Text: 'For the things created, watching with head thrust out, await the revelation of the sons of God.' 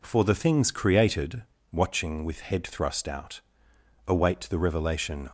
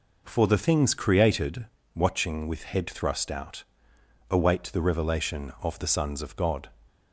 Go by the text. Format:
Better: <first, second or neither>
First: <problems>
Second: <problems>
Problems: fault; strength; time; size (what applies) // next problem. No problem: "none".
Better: second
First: stops before "of the sons of God"; at 5.2 s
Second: none